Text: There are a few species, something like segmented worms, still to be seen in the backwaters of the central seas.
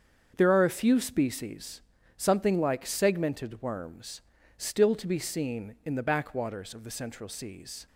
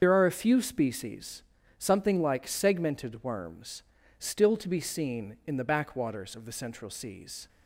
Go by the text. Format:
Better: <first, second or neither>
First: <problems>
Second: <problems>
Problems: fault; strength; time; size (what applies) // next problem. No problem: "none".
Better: first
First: starts louder than the rest; strong; until 1.3 s; 7 dB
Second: loses the start of "There"; at 0.0 s; 75 ms // starts louder than the rest; until 1.0 s; 7 dB